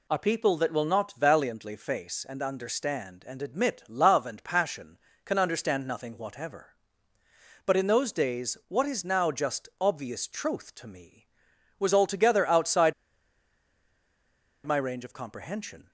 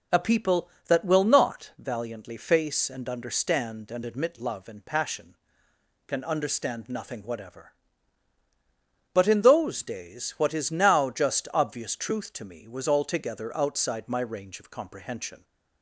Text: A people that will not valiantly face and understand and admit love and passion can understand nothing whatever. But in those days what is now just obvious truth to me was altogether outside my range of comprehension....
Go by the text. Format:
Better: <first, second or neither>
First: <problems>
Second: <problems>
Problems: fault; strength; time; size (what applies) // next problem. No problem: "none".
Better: second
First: pauses between "outside" and "my"; strong; at 12.9 s; 1.7 s long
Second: none